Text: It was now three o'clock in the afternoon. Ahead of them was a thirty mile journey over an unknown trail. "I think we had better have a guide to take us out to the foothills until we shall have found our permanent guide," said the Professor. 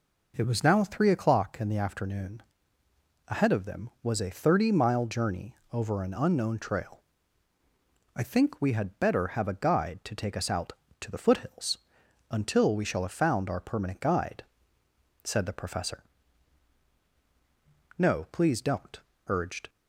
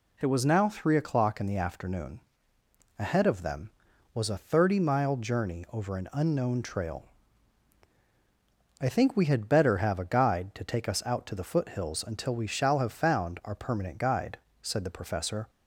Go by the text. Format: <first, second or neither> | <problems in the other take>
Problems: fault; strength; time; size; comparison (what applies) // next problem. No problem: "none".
second | pauses between "journey" and "over"; slight; at 5.5 s; 0.16 s long // pauses between "foothills" and "until"; noticeable; at 11.7 s; 0.54 s long // goes on to say "No please don't urged"; strong; from 17.9 s on; 1.7 s long